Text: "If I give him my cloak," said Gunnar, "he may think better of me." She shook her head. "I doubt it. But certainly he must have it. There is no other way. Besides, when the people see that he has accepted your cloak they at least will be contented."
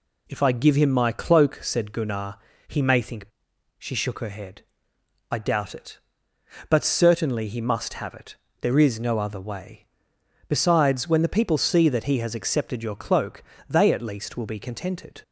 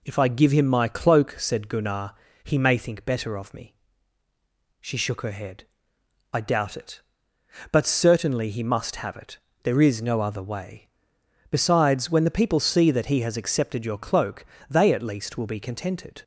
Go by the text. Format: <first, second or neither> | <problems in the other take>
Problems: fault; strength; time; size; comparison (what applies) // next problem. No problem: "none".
second | skips "better of me"; at 3.5 s // pauses between "cloak" and "they"; slight; at 13.4 s; 0.26 s long; slight in the second